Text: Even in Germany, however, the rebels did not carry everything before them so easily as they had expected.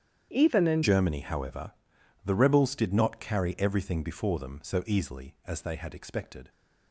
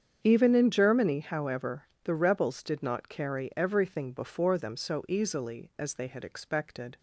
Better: second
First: starts louder than the rest; strong; until 1.3 s; 9 dB // changes voice at "Germany"; from 0.8 s on; 5.6 s long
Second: starts louder than the rest; strong; until 1.2 s; 7.5 dB

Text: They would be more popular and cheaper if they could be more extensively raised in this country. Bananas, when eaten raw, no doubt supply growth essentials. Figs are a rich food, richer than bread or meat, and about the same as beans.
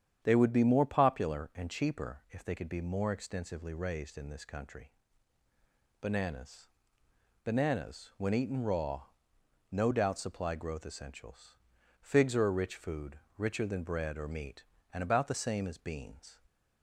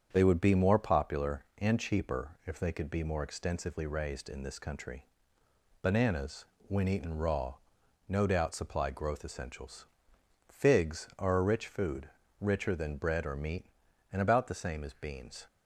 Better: second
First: starts louder than the rest; strong; until 1.2 s; 9 dB // says "Bananas" twice; at 7.4 s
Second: starts louder than the rest; strong; until 1.1 s; 7.5 dB

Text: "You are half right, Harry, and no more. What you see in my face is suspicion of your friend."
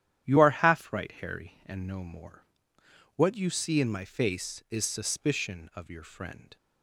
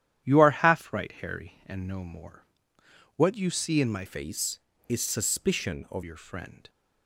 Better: first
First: starts louder than the rest; strong; until 1.3 s; 10.5 dB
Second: starts louder than the rest; strong; until 1.3 s; 11 dB // changes voice from "face" to "of"; from 4.0 to 6.0 s; 2.0 s long

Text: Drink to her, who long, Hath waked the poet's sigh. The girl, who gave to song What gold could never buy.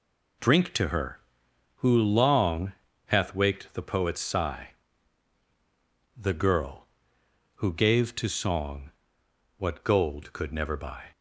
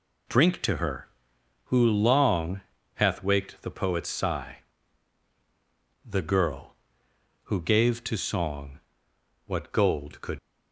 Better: first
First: pauses between "song" and "What"; noticeable; at 8.9 s; 0.68 s long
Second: pauses between "song" and "What"; noticeable; at 8.7 s; 0.68 s long // stops before "never buy"; at 10.3 s

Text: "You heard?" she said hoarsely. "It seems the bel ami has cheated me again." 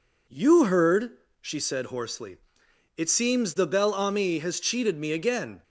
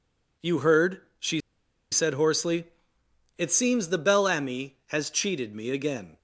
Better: first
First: none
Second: pauses between "she" and "said"; noticeable; at 1.4 s; 0.51 s long

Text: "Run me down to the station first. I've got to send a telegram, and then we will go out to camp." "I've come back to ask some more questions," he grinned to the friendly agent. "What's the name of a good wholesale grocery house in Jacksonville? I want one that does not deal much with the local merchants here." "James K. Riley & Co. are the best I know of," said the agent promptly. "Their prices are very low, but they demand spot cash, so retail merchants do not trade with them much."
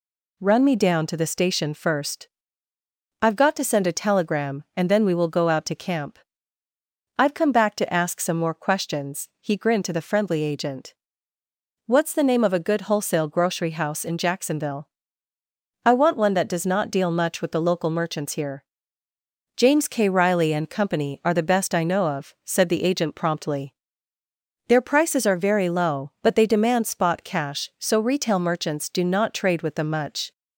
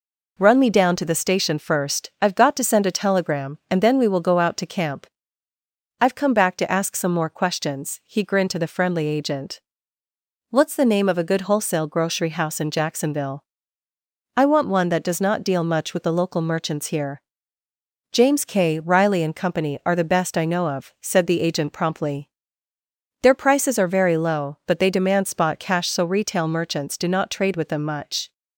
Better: neither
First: none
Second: none

